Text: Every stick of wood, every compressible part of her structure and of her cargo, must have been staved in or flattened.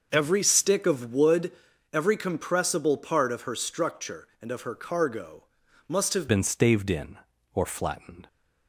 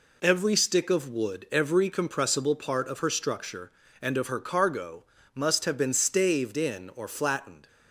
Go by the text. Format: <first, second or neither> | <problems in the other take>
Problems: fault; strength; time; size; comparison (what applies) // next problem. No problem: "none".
second | starts louder than the rest; noticeable; until 1.1 s; 6 dB // changes voice at "been"; from 6.2 s on; 2.0 s long